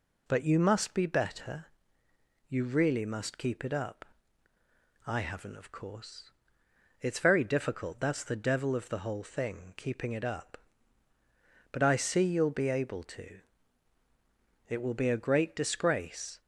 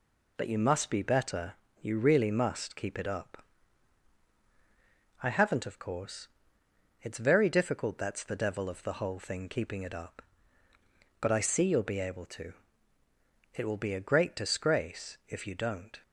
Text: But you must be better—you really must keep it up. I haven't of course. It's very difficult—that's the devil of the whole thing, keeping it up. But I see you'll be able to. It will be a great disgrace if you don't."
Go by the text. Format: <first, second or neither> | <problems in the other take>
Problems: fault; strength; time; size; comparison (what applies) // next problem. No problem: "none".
second | stops before "if you don't"; at 16.4 s